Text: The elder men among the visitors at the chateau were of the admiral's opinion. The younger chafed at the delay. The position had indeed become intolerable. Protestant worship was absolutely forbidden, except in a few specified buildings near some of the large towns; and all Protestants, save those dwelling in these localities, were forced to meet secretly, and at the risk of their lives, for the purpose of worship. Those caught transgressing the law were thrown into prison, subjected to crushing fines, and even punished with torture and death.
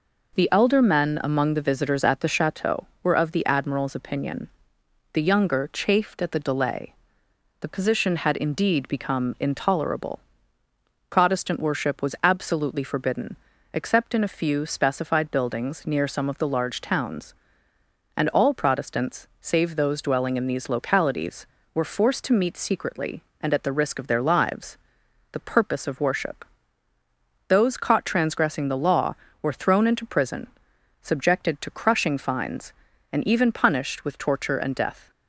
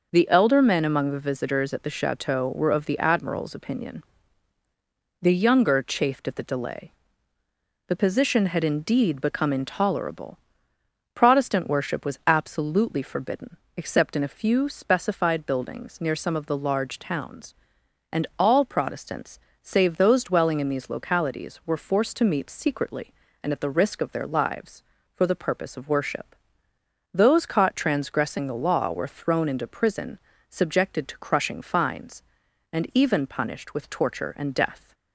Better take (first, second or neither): second